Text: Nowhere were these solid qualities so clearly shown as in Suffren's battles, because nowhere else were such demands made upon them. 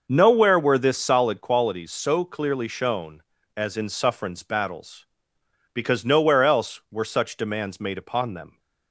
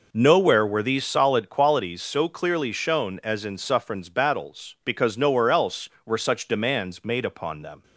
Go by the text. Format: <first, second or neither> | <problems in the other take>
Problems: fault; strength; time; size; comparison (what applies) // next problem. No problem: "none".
second | says "this" for "these"; at 0.7 s